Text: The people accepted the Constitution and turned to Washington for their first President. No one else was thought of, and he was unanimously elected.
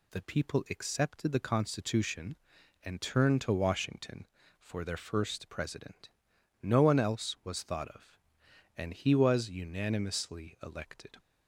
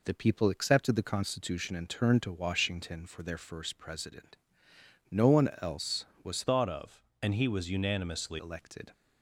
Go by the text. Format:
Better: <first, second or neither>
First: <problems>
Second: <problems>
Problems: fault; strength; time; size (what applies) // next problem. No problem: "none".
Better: first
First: none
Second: changes voice from "thought" to "unanimously"; from 6.4 to 8.3 s; 1.9 s long